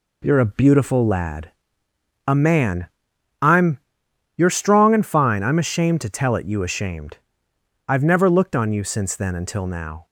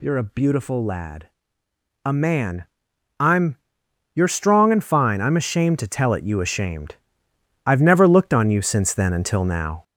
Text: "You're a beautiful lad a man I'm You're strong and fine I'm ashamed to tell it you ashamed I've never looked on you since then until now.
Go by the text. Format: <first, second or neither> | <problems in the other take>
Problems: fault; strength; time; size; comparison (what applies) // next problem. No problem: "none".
first | gets louder; noticeable; throughout; 5.5 dB // pauses between "lad" and "a"; noticeable; at 1.2 s; 0.74 s long; noticeable in the first // pauses between "man" and "I'm"; noticeable; at 2.6 s; 0.54 s long; noticeable in the first // pauses between "I'm" and "You're"; noticeable; at 3.5 s; 0.58 s long; noticeable in the first // pauses between "ashamed" and "I've"; noticeable; at 6.9 s; 0.72 s long; noticeable in the first